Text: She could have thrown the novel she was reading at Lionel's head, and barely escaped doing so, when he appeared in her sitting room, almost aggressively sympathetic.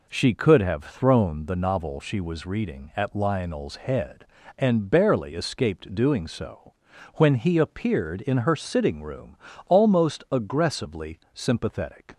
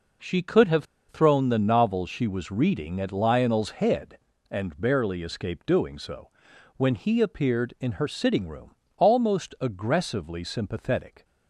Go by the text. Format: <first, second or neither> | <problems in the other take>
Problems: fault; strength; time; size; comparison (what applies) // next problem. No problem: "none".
first | pauses between "have" and "thrown"; slight; at 0.8 s; 0.25 s long